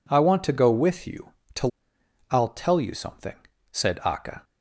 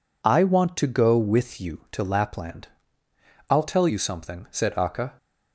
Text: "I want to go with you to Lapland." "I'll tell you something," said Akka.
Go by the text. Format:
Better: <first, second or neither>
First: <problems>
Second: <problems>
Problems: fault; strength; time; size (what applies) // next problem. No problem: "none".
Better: second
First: skips "Lapland"; at 1.9 s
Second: none